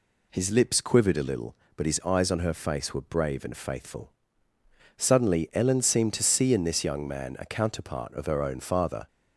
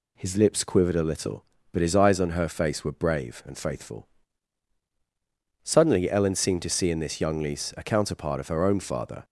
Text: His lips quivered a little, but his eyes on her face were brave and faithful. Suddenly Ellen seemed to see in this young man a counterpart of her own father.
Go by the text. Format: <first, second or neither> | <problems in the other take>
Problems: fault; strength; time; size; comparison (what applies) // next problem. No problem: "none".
first | says "lise" for "man"; at 7.4 s